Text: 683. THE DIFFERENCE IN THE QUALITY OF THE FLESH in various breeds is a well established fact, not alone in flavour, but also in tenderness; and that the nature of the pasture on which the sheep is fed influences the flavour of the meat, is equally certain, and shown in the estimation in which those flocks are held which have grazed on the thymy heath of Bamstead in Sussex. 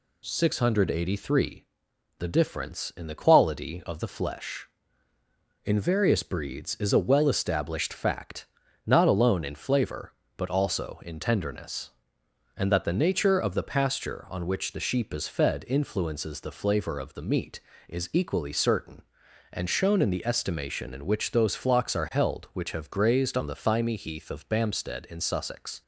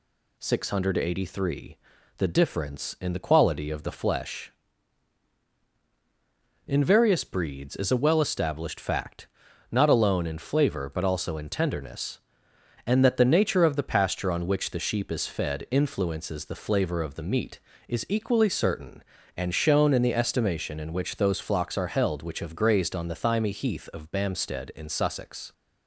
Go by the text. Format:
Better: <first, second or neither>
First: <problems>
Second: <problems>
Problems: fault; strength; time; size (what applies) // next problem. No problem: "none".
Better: neither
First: none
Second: none